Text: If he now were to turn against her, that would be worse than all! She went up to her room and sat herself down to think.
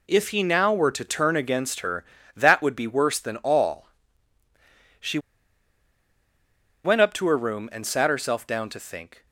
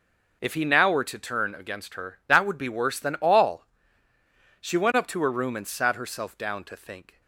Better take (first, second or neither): second